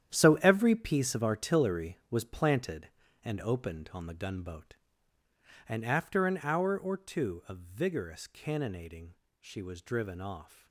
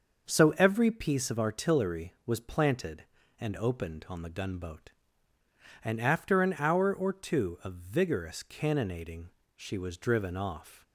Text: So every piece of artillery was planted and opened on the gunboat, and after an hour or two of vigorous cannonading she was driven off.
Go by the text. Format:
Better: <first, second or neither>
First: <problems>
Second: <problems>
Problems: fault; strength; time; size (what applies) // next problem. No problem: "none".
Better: second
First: gets quieter; strong; throughout; 12 dB // starts louder than the rest; strong; until 1.1 s; 10 dB // pauses between "cannonading" and "she"; slight; at 9.1 s; 0.26 s long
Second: starts louder than the rest; until 1.3 s; 6 dB // pauses between "cannonading" and "she"; slight; at 9.2 s; 0.26 s long